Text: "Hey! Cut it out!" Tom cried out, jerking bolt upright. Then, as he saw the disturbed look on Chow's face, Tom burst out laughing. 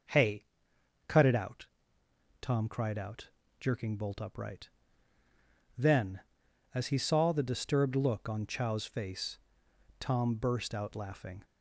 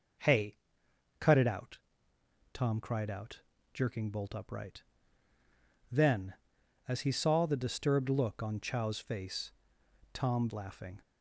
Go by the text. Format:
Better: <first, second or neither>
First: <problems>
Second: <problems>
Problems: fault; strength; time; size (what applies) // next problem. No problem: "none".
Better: first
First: none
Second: skips "burst out"; at 10.4 s